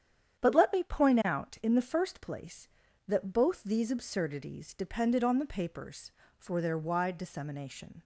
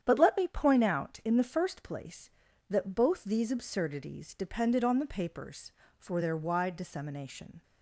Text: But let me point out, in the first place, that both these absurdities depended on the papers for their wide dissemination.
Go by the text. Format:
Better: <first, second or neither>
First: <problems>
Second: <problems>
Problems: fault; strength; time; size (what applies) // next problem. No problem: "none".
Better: neither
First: starts louder than the rest; strong; until 1.4 s; 9 dB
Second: starts louder than the rest; strong; until 1.0 s; 9 dB